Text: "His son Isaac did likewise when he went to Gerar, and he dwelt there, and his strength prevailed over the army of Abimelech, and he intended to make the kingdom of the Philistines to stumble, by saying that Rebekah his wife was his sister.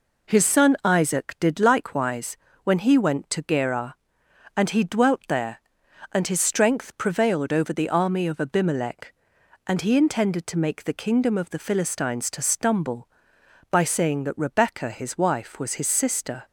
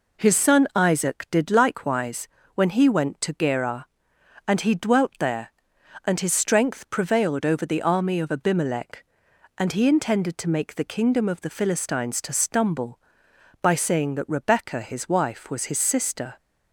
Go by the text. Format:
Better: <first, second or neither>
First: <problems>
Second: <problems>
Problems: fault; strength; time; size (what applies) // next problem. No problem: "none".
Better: neither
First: pauses between "likewise" and "when"; slight; at 2.3 s; 0.26 s long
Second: pauses between "likewise" and "when"; slight; at 2.2 s; 0.26 s long